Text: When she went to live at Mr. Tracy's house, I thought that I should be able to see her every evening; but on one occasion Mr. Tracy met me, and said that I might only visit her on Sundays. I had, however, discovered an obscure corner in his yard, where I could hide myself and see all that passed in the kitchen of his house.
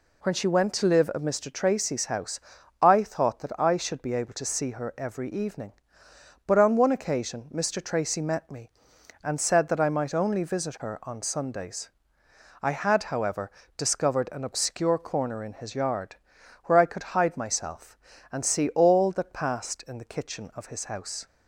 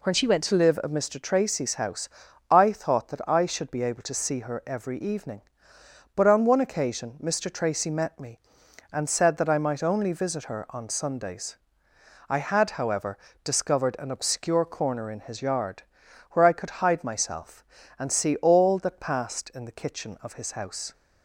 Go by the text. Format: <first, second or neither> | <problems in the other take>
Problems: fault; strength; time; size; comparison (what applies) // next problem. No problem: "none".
first | changes voice from "she" to "went"; from 0.1 to 0.4 s; 0.3 s long